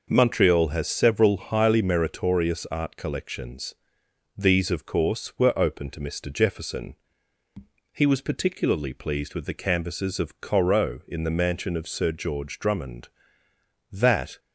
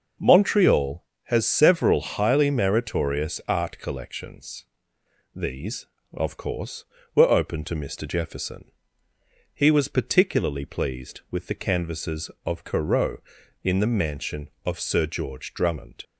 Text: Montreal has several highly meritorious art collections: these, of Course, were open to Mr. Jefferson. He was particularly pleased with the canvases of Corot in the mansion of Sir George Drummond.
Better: second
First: goes on to say "That"; slight; from 13.9 s on; 0.46 s long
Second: none

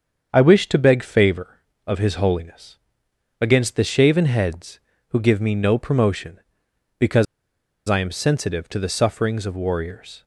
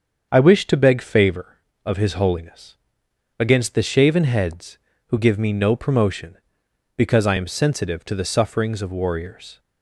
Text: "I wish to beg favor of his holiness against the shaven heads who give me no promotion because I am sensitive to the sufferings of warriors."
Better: second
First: starts louder than the rest; strong; until 1.3 s; 7 dB // pauses between "holiness" and "against"; noticeable; at 2.7 s; 0.62 s long // pauses between "because" and "I"; noticeable; at 7.2 s; 0.64 s long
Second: starts louder than the rest; strong; until 1.3 s; 7 dB // pauses between "holiness" and "against"; noticeable; at 2.7 s; 0.62 s long

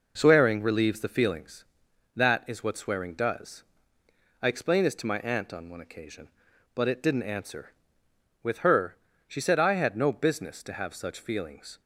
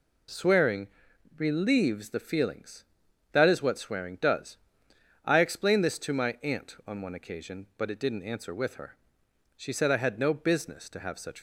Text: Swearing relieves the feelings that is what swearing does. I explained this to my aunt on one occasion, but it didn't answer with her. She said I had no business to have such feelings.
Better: first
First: none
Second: pauses between "Swearing" and "relieves"; noticeable; at 0.8 s; 0.52 s long // stops before "feelings"; at 11.3 s

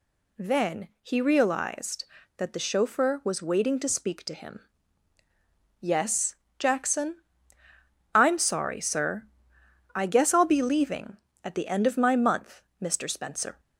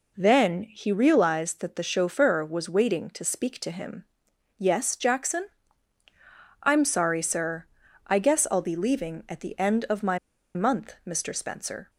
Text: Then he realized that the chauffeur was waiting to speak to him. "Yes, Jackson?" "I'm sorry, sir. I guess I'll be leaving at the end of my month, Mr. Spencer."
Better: first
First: none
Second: pauses between "my" and "month"; at 10.1 s; 0.37 s long

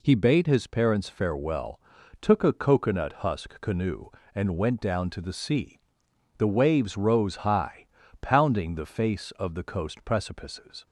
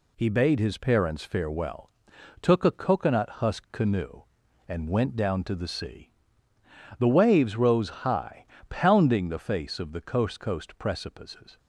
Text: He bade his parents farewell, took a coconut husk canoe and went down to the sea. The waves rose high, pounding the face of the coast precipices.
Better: first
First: none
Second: says "coast" twice; at 10.3 s

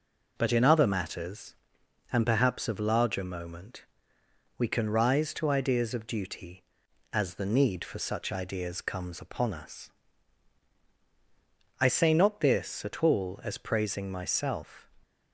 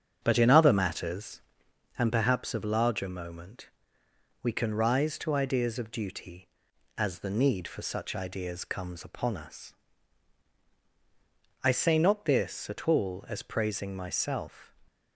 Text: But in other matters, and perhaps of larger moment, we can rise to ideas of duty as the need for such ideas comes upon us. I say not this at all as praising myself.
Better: first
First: none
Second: starts louder than the rest; strong; until 1.9 s; 7.5 dB

